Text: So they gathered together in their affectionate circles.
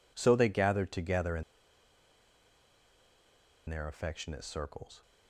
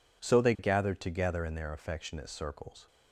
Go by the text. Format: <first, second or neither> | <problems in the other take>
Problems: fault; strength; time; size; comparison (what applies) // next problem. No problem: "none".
second | pauses between "in" and "their"; strong; at 1.4 s; 2.2 s long